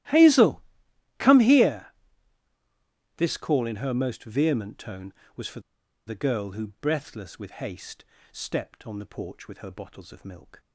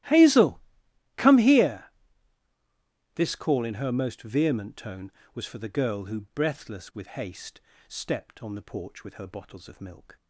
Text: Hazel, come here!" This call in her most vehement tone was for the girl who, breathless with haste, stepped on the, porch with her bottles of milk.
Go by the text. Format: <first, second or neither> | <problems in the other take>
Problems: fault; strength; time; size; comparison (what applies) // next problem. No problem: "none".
second | starts louder than the rest; strong; until 1.6 s; 15 dB; strong in the second // pauses between "for" and "the"; at 5.6 s; 0.45 s long